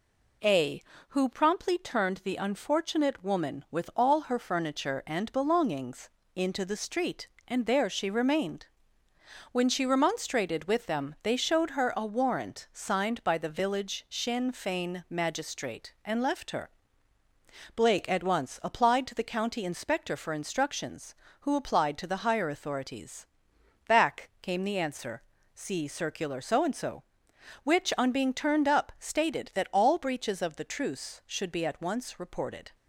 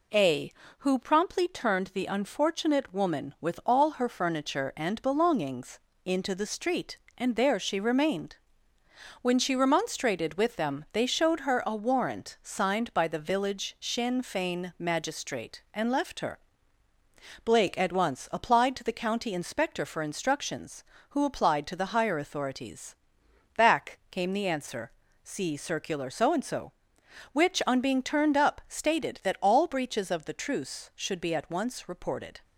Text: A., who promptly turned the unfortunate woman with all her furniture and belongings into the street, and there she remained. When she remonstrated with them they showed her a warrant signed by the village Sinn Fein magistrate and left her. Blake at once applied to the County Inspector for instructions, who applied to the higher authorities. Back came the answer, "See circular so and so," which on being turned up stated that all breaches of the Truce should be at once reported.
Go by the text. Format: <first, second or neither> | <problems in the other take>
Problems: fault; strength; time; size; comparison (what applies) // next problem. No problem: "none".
neither | pauses between "belongings" and "into"; slight; the same in both